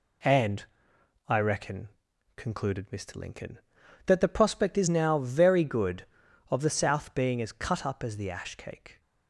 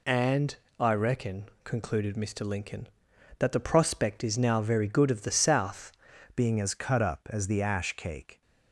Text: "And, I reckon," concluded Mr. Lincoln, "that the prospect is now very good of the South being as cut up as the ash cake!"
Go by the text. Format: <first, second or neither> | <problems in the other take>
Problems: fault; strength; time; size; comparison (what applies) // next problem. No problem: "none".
first | changes voice at "being"; from 6.3 s on; 2.1 s long